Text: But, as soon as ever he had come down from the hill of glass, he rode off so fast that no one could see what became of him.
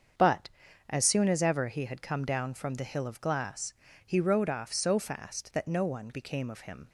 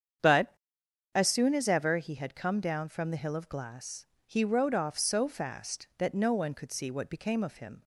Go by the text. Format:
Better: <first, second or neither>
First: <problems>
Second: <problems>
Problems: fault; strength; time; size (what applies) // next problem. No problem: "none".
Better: second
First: starts louder than the rest; until 1.5 s; 7 dB // skips "could see what"; at 6.1 s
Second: starts louder than the rest; strong; until 1.8 s; 8 dB